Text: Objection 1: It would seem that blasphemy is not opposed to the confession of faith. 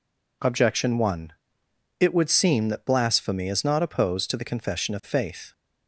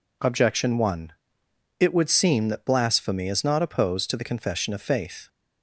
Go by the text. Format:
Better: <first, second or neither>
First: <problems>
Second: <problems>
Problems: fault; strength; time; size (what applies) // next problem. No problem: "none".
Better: neither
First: none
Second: none